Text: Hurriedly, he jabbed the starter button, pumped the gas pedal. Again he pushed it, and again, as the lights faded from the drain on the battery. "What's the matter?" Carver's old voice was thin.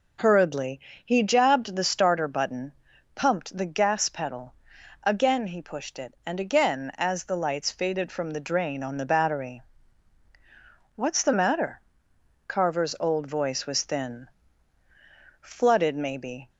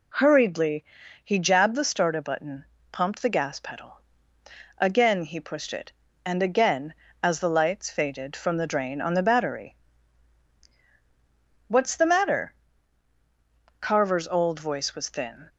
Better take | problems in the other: second | goes on to say "Flooded maybe"; noticeable; from 15.3 s on; 1.1 s long

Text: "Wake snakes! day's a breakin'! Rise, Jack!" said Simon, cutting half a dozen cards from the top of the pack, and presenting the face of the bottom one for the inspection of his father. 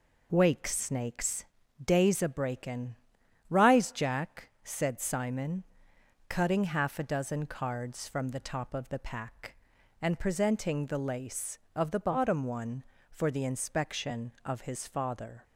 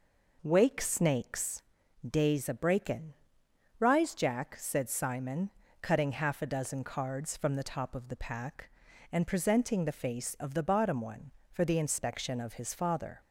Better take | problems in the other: second | says "lace" for "face"; at 10.9 s

